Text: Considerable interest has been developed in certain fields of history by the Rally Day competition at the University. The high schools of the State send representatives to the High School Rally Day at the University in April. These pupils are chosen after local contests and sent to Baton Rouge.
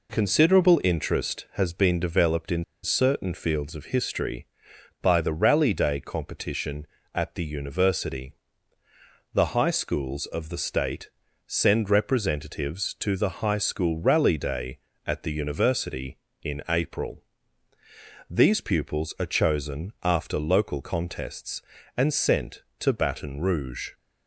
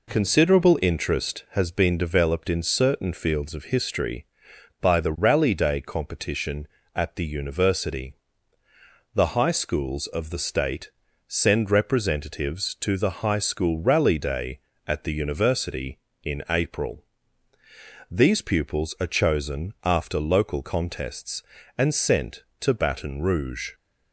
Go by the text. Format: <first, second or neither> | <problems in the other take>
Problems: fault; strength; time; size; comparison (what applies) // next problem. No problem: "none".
second | pauses between "in" and "certain"; slight; at 2.6 s; 0.19 s long // pauses between "State" and "send"; at 11.0 s; 0.38 s long; also in the second